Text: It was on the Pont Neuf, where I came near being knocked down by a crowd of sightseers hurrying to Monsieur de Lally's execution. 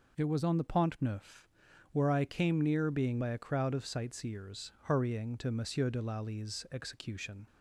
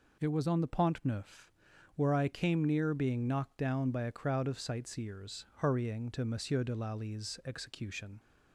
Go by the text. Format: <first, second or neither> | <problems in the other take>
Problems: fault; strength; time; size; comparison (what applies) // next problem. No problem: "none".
second | skips "knocked down"; at 3.2 s